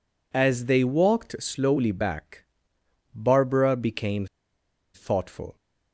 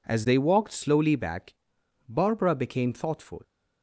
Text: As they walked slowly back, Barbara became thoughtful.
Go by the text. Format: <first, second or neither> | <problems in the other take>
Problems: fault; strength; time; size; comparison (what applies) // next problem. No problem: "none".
second | pauses between "became" and "thoughtful"; noticeable; at 4.2 s; 0.68 s long